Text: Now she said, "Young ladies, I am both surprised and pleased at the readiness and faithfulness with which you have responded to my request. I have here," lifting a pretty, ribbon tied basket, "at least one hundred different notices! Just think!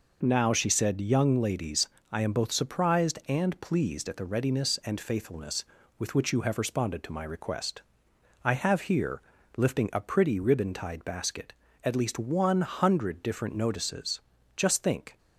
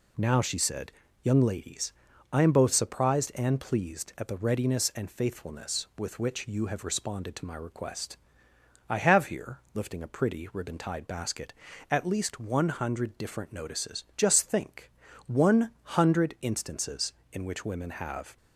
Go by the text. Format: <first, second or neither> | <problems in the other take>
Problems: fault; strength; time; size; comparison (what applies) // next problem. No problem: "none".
first | goes on to say "one hundred instances in which women have"; strong; from 15.2 s on; 3.1 s long